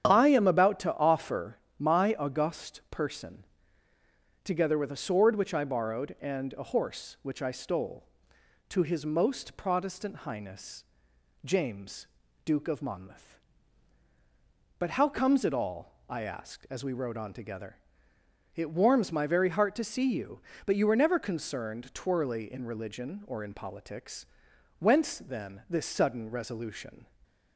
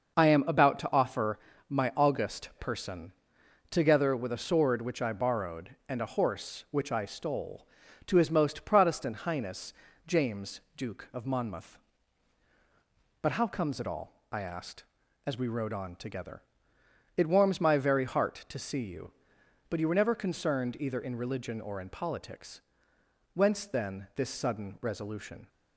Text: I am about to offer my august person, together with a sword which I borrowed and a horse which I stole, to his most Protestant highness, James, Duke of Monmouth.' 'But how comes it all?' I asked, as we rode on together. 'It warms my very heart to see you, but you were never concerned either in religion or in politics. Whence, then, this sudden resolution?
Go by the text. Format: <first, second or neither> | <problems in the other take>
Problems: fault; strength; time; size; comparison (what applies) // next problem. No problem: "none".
second | starts louder than the rest; strong; until 1.0 s; 8.5 dB; noticeable in the second // pauses between "offer" and "my"; slight; at 1.5 s; 0.22 s long; slight in the second // says "twirly" for "either"; at 21.9 s